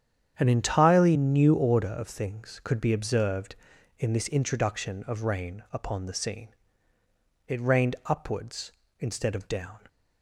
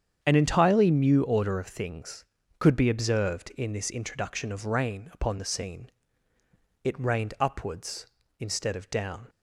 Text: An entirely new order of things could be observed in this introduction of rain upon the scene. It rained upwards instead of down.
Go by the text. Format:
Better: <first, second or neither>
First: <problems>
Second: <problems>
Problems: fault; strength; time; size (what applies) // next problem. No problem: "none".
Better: neither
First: starts louder than the rest; strong; until 1.3 s; 8.5 dB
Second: starts louder than the rest; strong; until 1.2 s; 8 dB